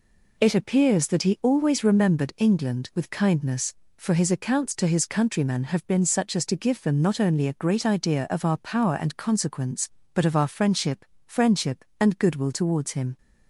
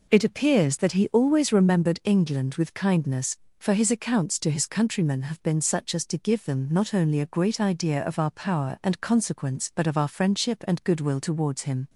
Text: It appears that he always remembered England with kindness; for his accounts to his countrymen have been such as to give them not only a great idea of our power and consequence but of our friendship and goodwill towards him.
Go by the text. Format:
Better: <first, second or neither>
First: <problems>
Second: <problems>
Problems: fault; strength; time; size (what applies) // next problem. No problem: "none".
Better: second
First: says "friendship" twice; at 11.2 s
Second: none